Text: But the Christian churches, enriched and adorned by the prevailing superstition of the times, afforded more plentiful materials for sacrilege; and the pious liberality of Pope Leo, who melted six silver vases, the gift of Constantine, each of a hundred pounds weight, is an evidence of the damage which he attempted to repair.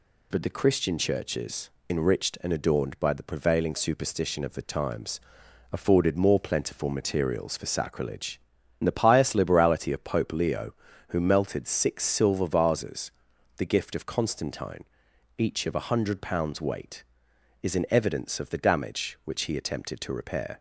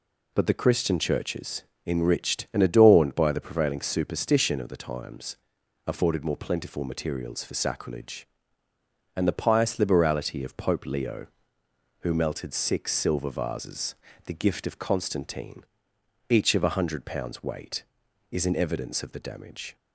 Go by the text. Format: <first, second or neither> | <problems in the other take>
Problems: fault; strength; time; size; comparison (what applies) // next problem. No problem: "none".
first | stops before "which he attempted to repair"; at 19.7 s